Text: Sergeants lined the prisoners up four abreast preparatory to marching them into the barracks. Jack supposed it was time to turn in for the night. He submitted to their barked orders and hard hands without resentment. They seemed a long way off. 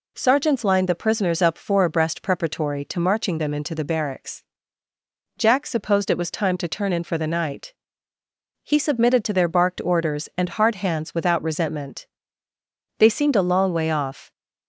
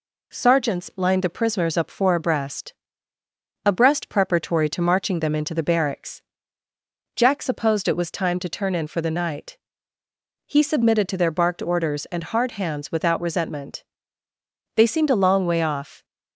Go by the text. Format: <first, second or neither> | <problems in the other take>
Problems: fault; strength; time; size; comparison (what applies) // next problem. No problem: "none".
first | says "abreast" twice; at 3.6 s